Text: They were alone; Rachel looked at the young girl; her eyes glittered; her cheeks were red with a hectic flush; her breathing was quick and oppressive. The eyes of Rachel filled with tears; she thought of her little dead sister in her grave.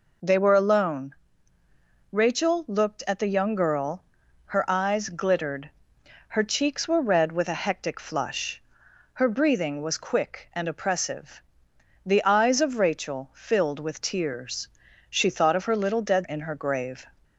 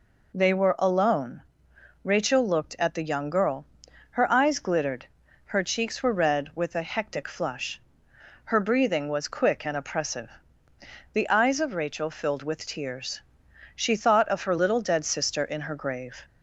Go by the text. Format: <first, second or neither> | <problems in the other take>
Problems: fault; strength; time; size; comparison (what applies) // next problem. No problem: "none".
second | skips "sister"; at 16.2 s